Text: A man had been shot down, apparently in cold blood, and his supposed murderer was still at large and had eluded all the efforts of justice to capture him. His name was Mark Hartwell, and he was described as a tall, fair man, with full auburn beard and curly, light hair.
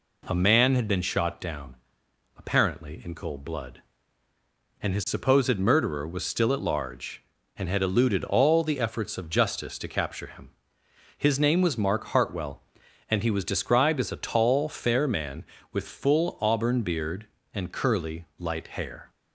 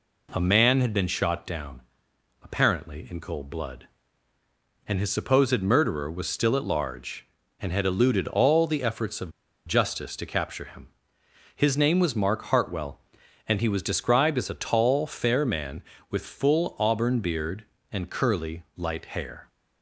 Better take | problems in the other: first | pauses between "of" and "justice"; slight; at 9.3 s; 0.34 s long

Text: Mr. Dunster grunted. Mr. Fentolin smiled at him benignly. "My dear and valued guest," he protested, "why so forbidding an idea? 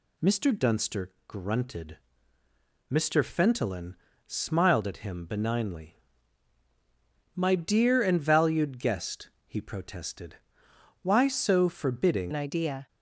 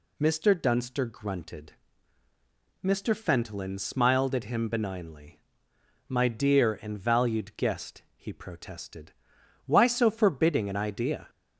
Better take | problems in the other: second | pauses between "Dunster" and "grunted"; slight; at 1.1 s; 0.16 s long // pauses between "Fentolin" and "smiled"; slight; at 3.9 s; 0.32 s long // changes voice at "an"; from 12.3 s on; 0.5 s long

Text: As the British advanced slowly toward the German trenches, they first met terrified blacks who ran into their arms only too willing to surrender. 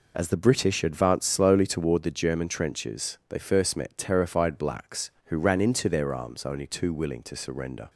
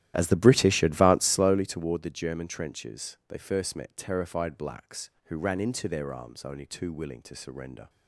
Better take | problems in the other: first | starts louder than the rest; strong; until 1.6 s; 13 dB

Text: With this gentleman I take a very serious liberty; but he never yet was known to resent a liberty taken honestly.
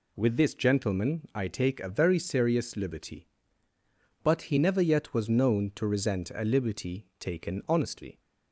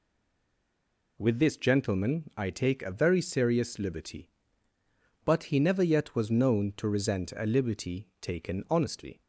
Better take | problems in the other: first | stays silent before the first word; noticeable; until 1.1 s; 1.1 s long

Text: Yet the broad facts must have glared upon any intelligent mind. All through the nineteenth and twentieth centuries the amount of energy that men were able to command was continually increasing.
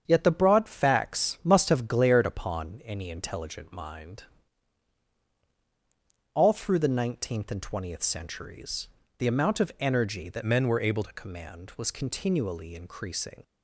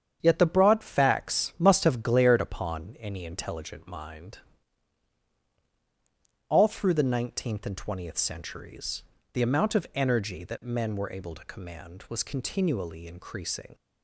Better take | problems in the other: second | starts louder than the rest; strong; until 1.0 s; 8 dB; strong in the second // pauses between "centuries" and "the"; slight; at 8.8 s; 0.30 s long; slight in the second // changes voice from "men" to "able"; from 10.4 to 11.0 s; 0.6 s long

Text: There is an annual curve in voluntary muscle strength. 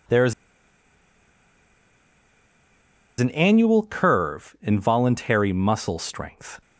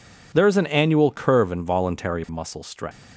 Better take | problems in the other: second | pauses between "is" and "an"; strong; at 0.3 s; 2.8 s long

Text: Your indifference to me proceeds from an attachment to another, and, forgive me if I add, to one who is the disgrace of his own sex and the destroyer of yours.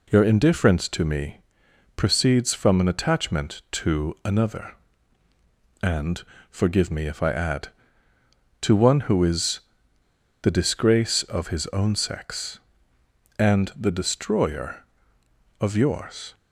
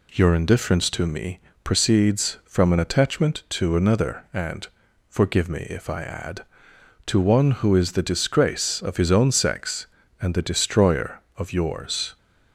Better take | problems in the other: second | pauses between "me" and "proceeds"; noticeable; at 1.4 s; 0.54 s long; slight in the second // pauses between "is" and "the"; noticeable; at 9.6 s; 0.81 s long

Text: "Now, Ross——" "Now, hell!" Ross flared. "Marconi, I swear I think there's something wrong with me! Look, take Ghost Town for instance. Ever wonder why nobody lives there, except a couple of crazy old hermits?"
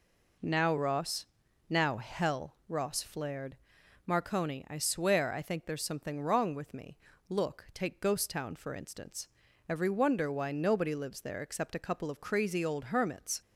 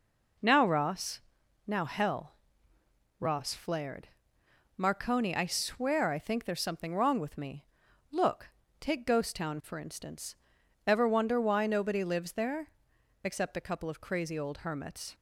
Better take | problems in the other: second | says "Every" for "Ever"; at 9.6 s

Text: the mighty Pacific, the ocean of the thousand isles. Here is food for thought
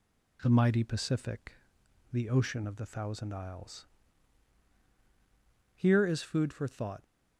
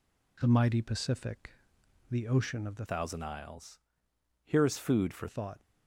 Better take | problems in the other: first | changes voice from "thousand" to "for"; from 2.8 to 5.2 s; 2.4 s long

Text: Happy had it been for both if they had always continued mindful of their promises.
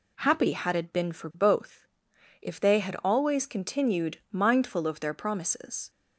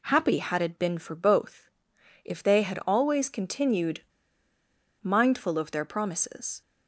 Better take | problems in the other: first | pauses between "both" and "if"; noticeable; at 1.6 s; 0.54 s long; noticeable in the first // pauses between "continued" and "mindful"; at 4.0 s; 1.0 s long

